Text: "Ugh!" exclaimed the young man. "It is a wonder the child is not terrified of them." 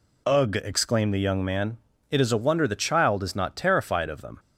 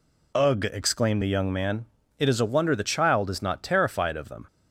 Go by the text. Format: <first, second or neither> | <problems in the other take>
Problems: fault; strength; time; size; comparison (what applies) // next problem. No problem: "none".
neither | none